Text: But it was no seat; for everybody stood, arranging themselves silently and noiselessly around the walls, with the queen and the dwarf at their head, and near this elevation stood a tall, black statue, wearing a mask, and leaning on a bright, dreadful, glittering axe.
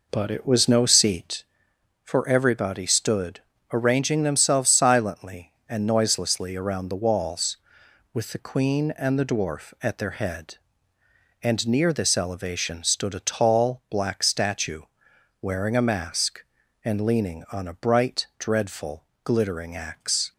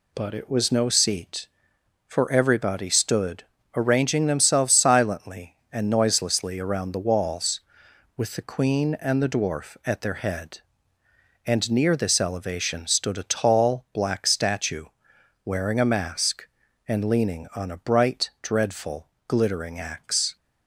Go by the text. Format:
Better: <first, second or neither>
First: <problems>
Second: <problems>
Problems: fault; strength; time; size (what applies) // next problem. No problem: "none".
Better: second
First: starts louder than the rest; noticeable; until 1.4 s; 4.5 dB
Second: none